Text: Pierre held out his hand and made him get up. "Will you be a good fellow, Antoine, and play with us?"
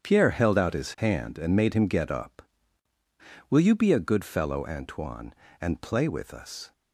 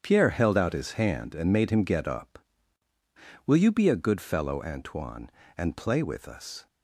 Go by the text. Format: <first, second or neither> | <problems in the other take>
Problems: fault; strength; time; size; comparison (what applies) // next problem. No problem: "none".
neither | starts louder than the rest; strong; the same in both